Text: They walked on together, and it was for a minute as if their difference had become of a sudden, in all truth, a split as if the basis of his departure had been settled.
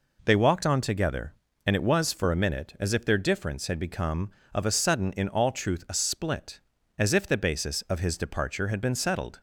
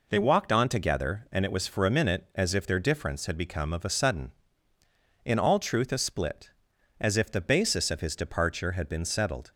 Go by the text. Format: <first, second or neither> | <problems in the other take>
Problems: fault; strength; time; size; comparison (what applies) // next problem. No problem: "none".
neither | none